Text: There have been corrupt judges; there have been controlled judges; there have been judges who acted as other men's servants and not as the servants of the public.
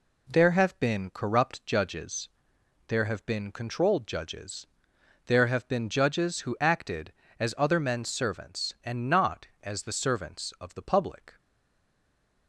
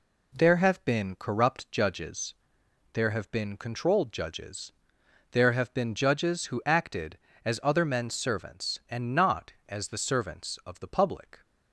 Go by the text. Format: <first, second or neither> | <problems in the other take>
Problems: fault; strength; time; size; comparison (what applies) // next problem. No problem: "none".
second | stays silent after the last word; from 11.3 s on; 1.1 s long